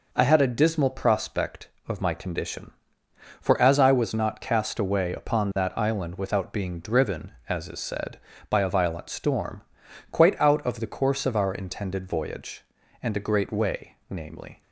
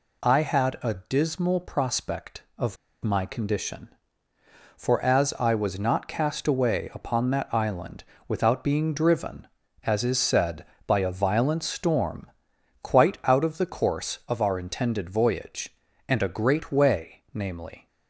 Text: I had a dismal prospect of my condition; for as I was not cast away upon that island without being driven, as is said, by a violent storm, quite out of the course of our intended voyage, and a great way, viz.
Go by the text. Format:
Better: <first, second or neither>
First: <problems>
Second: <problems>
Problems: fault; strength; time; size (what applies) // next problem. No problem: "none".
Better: first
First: none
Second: pauses between "of" and "my"; slight; at 2.7 s; 0.28 s long // pauses between "island" and "without"; slight; at 8.0 s; 0.24 s long